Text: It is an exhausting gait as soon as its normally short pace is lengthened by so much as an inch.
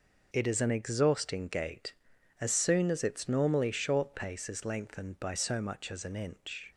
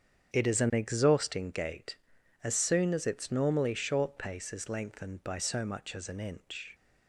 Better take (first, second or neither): first